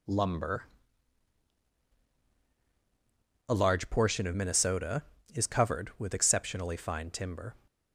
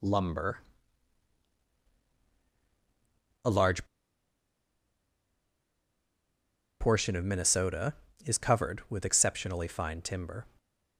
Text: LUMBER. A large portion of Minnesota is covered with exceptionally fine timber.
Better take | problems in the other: first | pauses between "large" and "portion"; strong; at 3.8 s; 2.9 s long

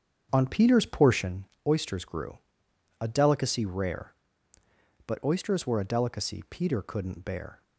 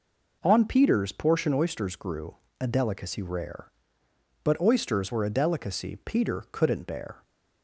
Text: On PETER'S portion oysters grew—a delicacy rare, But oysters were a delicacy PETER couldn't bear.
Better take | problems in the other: second | starts louder than the rest; strong; until 1.4 s; 7.5 dB // pauses between "portion" and "oysters"; slight; at 1.4 s; 0.20 s long

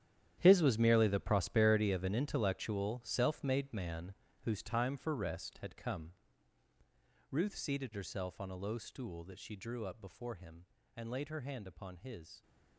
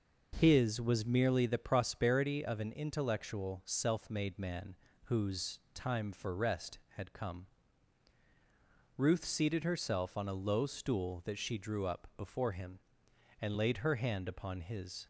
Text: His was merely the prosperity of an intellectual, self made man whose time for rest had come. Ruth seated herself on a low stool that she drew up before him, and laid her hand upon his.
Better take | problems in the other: second | gets quieter; strong; throughout; 14.5 dB // pauses between "man" and "whose"; slight; at 4.1 s; 0.30 s long; slight in the second

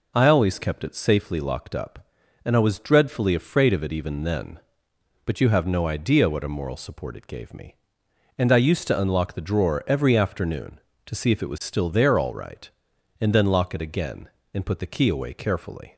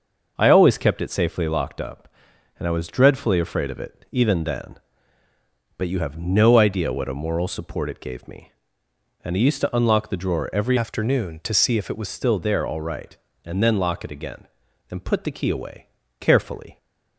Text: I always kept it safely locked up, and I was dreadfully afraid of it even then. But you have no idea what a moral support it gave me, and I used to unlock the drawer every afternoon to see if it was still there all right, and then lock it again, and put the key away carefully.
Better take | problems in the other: first | starts louder than the rest; noticeable; until 1.3 s; 6 dB // changes voice from "afternoon" to "was"; from 10.7 to 12.0 s; 1.3 s long // pauses between "away" and "carefully"; slight; at 15.8 s; 0.32 s long

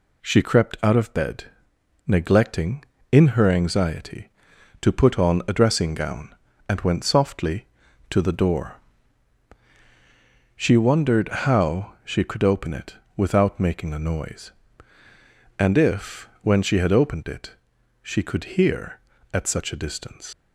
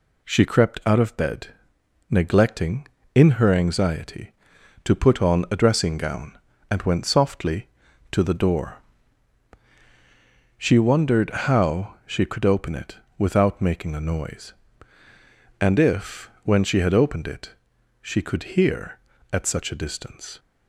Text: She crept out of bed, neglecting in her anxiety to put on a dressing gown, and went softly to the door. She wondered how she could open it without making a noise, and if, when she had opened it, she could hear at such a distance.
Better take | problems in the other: second | pauses between "it" and "without"; slight; at 12.9 s; 0.22 s long; slight in the second // leaves "distance" unfinished; at 20.3 s; 65 ms

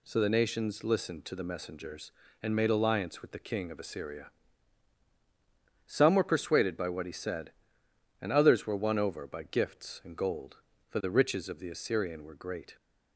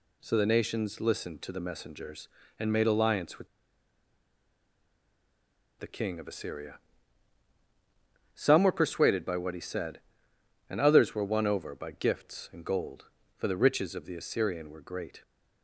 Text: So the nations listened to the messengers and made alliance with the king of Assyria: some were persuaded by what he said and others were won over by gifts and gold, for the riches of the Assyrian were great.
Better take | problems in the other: first | pauses between "with" and "the"; strong; at 3.4 s; 2.3 s long

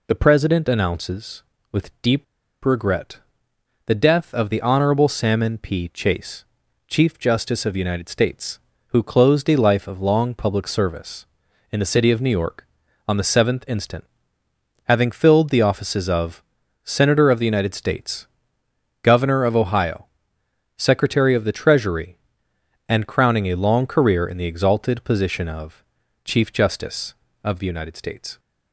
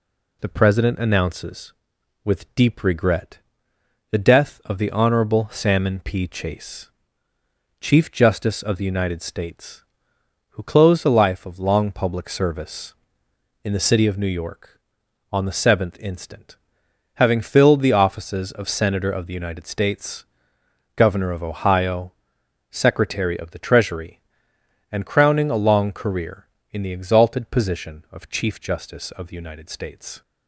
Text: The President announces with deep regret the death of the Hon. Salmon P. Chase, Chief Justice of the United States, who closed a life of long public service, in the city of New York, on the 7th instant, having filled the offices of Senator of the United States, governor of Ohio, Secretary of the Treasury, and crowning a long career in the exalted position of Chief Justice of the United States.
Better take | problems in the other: second | pauses between "deep" and "regret"; at 2.2 s; 0.40 s long // pauses between "regret" and "the"; noticeable; at 3.1 s; 0.66 s long; noticeable in the second // pauses between "of" and "Senator"; at 16.4 s; 0.40 s long // pauses between "of" and "Chief"; at 25.8 s; 0.42 s long

